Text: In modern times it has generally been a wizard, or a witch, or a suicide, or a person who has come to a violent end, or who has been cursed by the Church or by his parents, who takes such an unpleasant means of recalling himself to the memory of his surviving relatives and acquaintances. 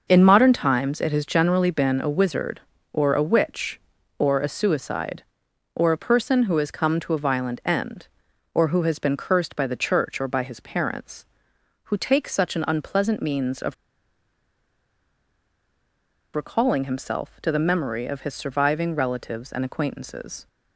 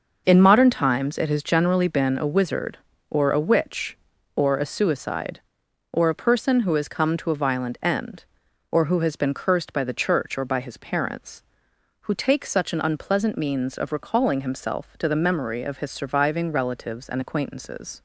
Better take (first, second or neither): second